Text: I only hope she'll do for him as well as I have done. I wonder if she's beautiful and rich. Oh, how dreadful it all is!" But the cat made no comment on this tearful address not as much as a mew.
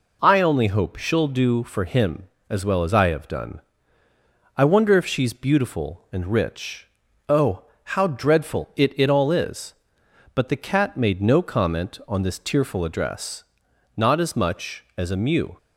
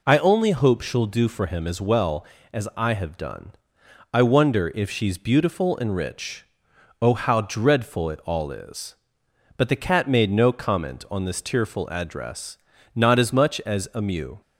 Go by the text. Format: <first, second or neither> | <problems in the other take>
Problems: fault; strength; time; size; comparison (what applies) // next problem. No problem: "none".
second | says "it" twice; at 8.9 s // pauses between "address" and "not"; noticeable; at 13.4 s; 0.52 s long; also in the second